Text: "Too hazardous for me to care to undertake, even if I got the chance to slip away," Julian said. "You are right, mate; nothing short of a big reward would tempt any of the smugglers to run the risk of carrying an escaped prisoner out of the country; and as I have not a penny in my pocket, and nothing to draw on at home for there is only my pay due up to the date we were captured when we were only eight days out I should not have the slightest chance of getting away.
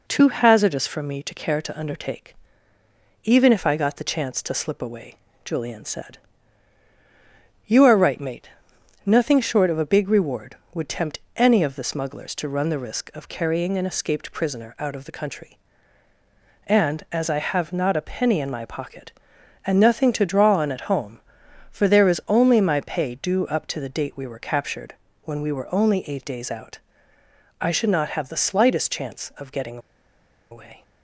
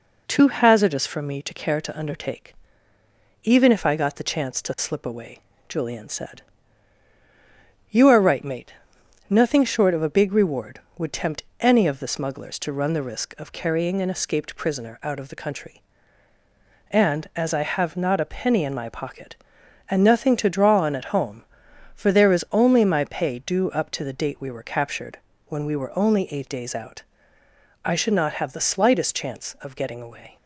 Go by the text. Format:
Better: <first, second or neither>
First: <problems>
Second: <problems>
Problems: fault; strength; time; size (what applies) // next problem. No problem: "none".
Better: second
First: pauses between "tempt" and "any"; slight; at 11.1 s; 0.16 s long // pauses between "captured" and "when"; slight; at 24.9 s; 0.30 s long // pauses between "out" and "I"; noticeable; at 26.7 s; 0.80 s long // pauses between "getting" and "away"; noticeable; at 29.7 s; 0.72 s long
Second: pauses between "tempt" and "any"; slight; at 11.4 s; 0.16 s long // pauses between "captured" and "when"; slight; at 25.1 s; 0.30 s long // pauses between "out" and "I"; noticeable; at 27.0 s; 0.80 s long